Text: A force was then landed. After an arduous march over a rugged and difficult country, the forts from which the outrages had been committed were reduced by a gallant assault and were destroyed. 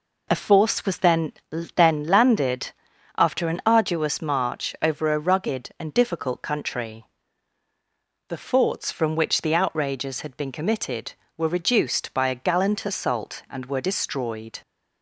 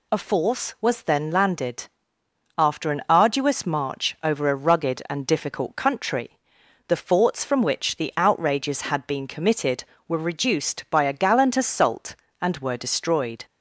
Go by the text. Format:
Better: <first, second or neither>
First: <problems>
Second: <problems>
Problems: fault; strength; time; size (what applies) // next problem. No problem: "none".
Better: second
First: says "then" twice; at 1.7 s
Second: none